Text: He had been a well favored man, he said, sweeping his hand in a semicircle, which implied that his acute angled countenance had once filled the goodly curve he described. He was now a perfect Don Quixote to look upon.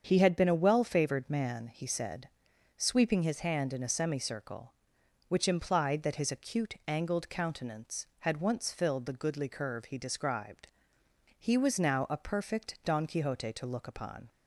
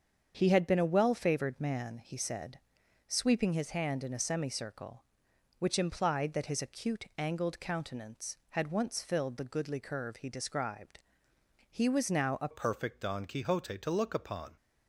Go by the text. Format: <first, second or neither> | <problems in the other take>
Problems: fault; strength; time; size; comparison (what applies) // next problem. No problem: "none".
first | starts louder than the rest; until 1.3 s; 7 dB; also in the first // changes voice at "perfect"; from 12.5 s on; 2.0 s long